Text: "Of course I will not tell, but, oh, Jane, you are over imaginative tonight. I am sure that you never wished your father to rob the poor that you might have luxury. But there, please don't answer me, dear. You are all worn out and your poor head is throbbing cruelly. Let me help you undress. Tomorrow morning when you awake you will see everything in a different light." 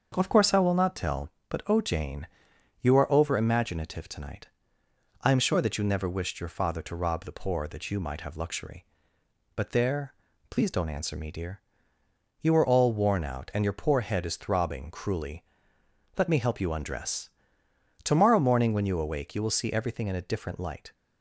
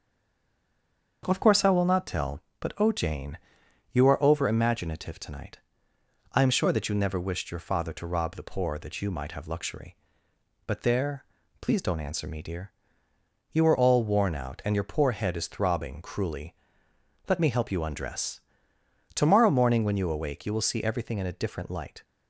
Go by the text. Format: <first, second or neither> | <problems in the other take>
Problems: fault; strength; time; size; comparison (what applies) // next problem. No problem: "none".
first | stays silent before the first word; noticeable; until 1.2 s; 1.2 s long // starts louder than the rest; until 2.2 s; 6.5 dB; also in the first